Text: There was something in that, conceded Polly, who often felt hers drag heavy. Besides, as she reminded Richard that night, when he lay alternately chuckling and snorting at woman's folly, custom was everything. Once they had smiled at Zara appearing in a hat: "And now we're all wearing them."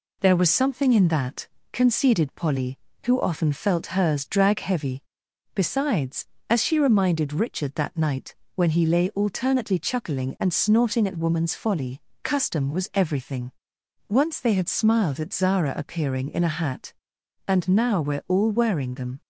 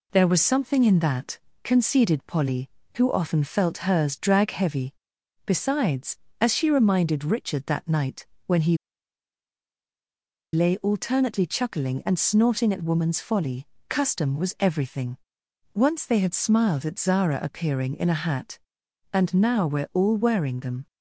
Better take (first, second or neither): first